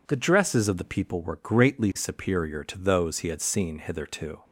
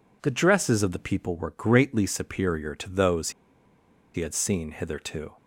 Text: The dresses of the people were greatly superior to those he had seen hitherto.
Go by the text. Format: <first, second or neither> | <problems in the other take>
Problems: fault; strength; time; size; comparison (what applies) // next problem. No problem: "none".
first | pauses between "those" and "he"; noticeable; at 3.2 s; 0.84 s long